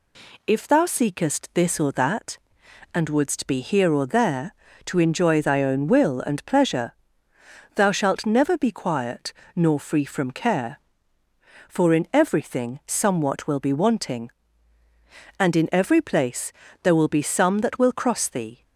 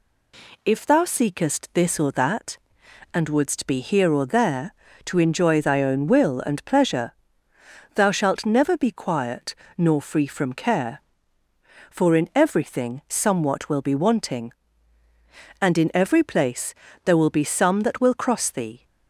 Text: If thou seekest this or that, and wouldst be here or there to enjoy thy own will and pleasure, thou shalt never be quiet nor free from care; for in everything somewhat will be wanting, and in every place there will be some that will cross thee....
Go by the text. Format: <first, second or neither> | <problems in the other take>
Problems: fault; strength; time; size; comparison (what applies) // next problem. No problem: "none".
neither | pauses between "quiet" and "nor"; slight; the same in both // pauses between "place" and "there"; slight; the same in both